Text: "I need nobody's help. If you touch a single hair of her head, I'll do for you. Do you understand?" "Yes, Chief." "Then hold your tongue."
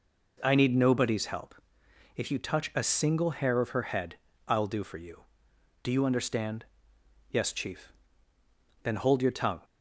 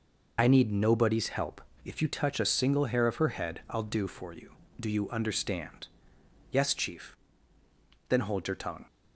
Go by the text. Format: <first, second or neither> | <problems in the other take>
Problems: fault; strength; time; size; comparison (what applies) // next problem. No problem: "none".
first | loses the start of "I"; at 0.3 s; 30 ms